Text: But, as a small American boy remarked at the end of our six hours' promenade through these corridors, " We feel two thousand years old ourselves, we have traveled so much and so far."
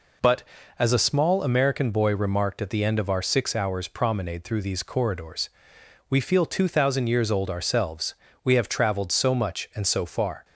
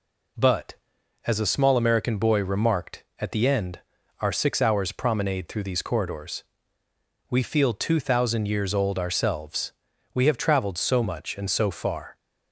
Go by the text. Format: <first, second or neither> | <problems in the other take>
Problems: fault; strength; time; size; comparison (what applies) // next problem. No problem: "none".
first | skips "of"; at 3.9 s